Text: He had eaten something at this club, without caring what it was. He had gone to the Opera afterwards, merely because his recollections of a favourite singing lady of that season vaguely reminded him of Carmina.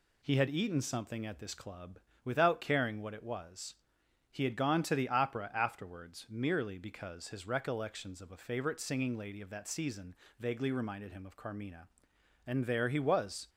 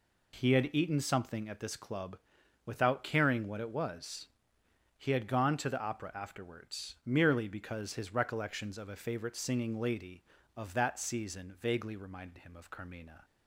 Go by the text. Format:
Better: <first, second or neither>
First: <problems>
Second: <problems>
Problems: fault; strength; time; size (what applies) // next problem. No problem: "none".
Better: second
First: pauses between "season" and "vaguely"; slight; at 10.1 s; 0.24 s long // goes on to say "And there he was"; noticeable; from 12.4 s on; 1.0 s long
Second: none